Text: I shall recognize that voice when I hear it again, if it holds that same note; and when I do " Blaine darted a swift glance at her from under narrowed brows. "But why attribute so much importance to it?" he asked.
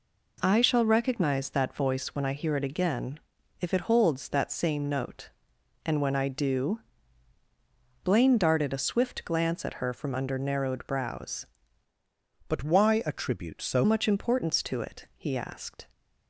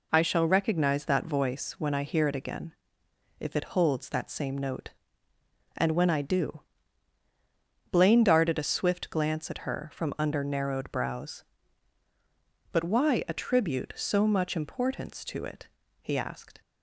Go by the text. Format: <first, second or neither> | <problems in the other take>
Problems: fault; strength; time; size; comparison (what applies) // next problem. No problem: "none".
second | changes voice from "But" to "so"; from 12.4 to 13.8 s; 1.4 s long